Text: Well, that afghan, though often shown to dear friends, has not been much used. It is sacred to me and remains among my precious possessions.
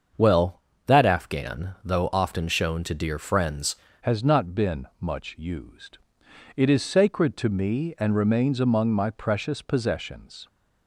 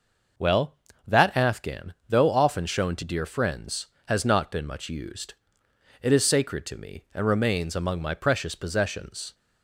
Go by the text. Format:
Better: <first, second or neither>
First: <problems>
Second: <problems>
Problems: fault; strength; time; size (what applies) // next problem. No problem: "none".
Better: second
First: starts louder than the rest; until 1.4 s; 6.5 dB // changes voice at "has"; from 4.0 s on; 6.4 s long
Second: none